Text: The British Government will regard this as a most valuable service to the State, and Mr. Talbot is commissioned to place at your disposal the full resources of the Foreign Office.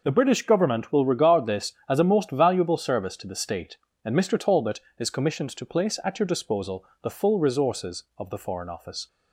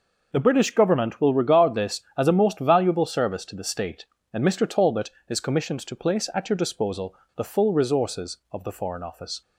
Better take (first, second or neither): neither